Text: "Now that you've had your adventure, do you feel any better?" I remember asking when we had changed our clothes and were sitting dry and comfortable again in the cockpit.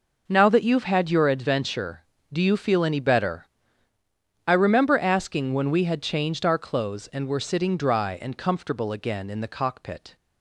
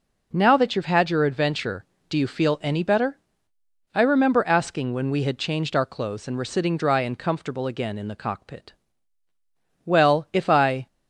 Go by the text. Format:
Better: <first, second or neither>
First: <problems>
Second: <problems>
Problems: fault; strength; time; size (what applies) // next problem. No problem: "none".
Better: first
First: none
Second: goes on to say "Well if I"; noticeable; from 9.8 s on; 1.0 s long